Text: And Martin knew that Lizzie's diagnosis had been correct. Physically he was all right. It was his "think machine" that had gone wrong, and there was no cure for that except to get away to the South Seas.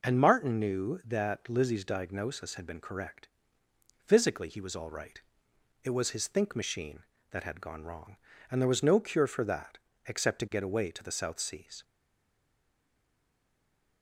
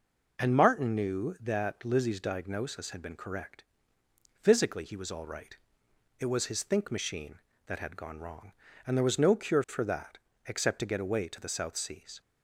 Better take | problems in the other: second | pauses between "that" and "except"; slight; at 9.7 s; 0.28 s long; slight in the second // stays silent after the last word; from 11.8 s on; 2.2 s long

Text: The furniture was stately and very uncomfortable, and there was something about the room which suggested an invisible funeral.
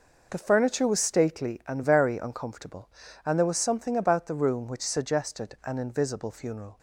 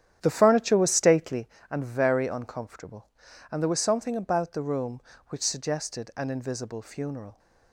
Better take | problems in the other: first | starts louder than the rest; strong; until 1.5 s; 10 dB

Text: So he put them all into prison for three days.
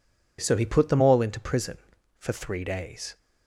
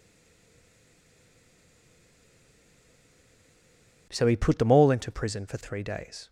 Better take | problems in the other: first | stays silent before the first word; strong; until 4.0 s; 4.0 s long

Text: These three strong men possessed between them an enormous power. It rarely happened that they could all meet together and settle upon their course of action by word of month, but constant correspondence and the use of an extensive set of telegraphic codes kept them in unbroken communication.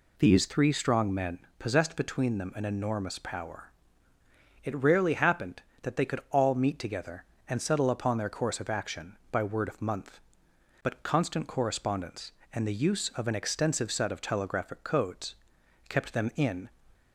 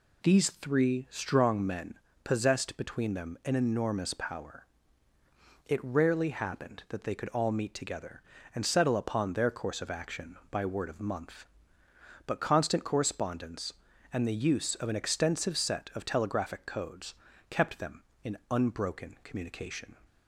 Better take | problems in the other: second | pauses between "men" and "possessed"; slight; at 1.4 s; 0.18 s long; slight in the second // pauses between "codes" and "kept"; noticeable; at 15.3 s; 0.54 s long; slight in the second // stops before "unbroken communication"; at 16.9 s

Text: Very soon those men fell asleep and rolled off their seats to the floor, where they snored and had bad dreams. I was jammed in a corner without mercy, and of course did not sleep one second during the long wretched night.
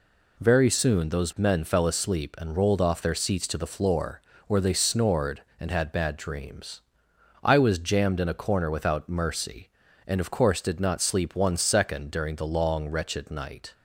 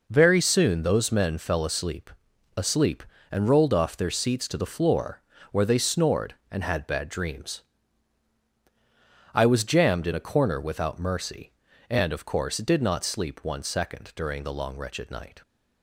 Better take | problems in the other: first | says "asleep" twice; at 2.5 s

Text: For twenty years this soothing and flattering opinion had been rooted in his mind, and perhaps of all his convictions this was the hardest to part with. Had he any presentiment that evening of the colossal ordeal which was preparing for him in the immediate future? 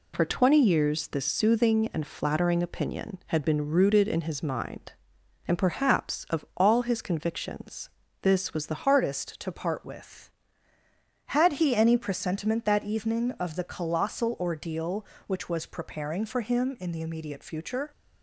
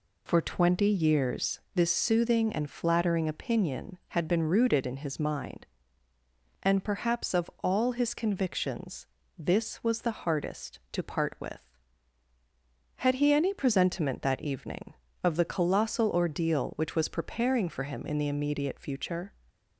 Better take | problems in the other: second | pauses between "convictions" and "this"; slight; at 7.8 s; 0.32 s long; slight in the second // changes voice at "hardest"; from 8.8 s on; 9.1 s long

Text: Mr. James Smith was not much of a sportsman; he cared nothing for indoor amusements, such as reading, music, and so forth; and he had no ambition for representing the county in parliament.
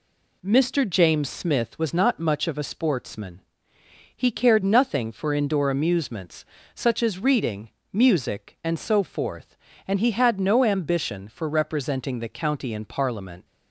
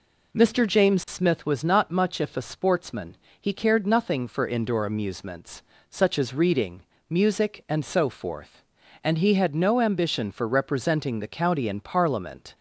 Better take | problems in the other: first | says "if" for "of"; at 2.1 s

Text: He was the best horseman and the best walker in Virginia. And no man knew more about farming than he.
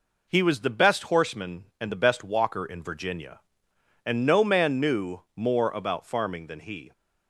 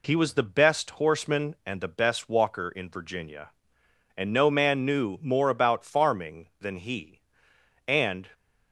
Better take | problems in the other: first | goes on to say "And"; slight; from 7.8 s on; 0.42 s long

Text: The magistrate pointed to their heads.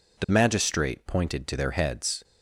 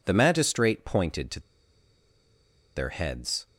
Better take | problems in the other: first | pauses between "to" and "their"; strong; at 1.3 s; 1.3 s long

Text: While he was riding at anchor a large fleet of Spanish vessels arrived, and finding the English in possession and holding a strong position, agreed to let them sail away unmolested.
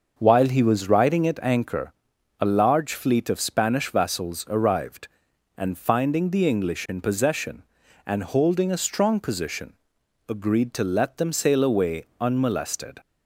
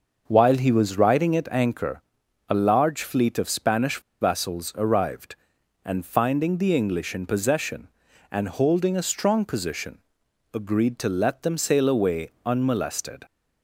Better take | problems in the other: first | starts louder than the rest; until 1.2 s; 6 dB; also in the first // pauses between "anchor" and "a"; noticeable; at 2.0 s; 0.48 s long; noticeable in the first // pauses between "Spanish" and "vessels"; slight; at 3.9 s; 0.21 s long // pauses between "away" and "unmolested"; slight; at 12.2 s; 0.16 s long; slight in the first

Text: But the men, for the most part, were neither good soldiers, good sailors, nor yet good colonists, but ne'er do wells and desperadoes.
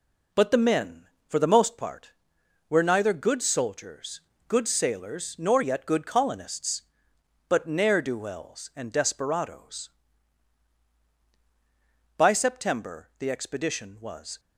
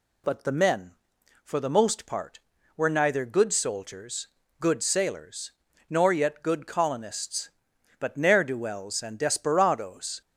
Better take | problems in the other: second | goes on to say "By September the expedition was"; strong; from 12.1 s on; 2.2 s long

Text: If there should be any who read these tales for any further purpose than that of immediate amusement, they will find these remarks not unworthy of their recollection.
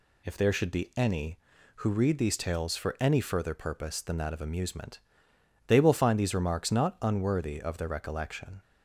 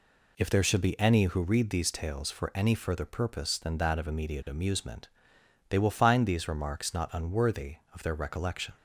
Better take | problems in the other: second | skips "immediate"; at 4.4 s

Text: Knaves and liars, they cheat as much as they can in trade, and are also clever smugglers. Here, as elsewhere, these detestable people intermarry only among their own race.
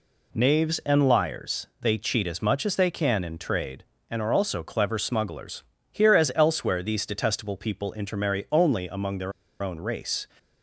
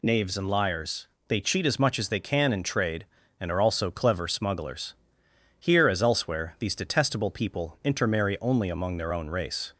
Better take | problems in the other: second | pauses between "their" and "own"; slight; at 9.3 s; 0.30 s long

